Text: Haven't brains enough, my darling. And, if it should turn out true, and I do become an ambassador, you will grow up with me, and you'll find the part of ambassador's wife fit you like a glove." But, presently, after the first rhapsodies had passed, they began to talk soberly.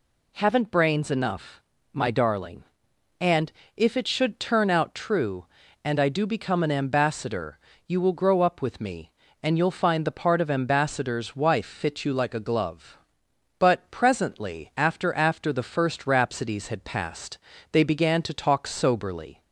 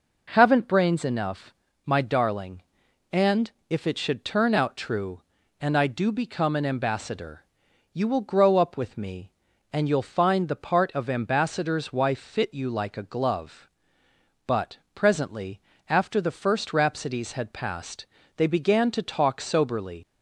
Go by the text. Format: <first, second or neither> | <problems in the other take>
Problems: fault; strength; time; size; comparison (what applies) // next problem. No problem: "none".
second | says "after" twice; at 15.1 s